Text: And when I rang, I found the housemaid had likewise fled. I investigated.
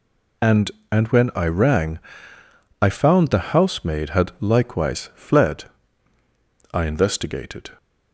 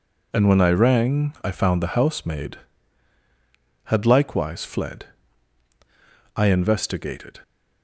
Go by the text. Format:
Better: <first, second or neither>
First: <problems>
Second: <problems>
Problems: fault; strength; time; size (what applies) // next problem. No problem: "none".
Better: second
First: says "And" twice; at 0.9 s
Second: none